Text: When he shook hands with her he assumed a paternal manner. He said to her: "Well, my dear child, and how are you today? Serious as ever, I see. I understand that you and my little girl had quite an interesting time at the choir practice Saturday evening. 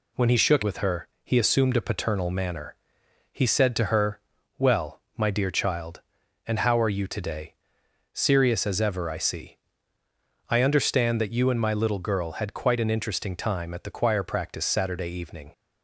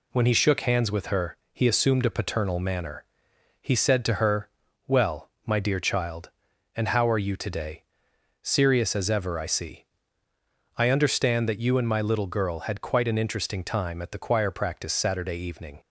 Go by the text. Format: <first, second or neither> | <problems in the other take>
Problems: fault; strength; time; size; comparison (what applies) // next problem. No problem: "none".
second | skips "hands"; at 0.6 s // pauses between "her" and "he"; slight; at 1.0 s; 0.16 s long; slight in the second